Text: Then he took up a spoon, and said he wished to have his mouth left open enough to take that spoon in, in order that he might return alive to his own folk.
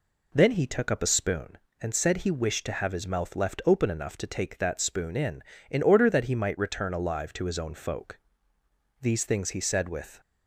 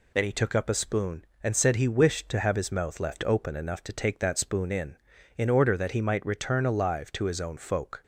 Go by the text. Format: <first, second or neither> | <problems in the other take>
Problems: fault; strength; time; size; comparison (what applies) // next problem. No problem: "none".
second | goes on to say "These things he said with"; noticeable; from 9.0 s on; 1.1 s long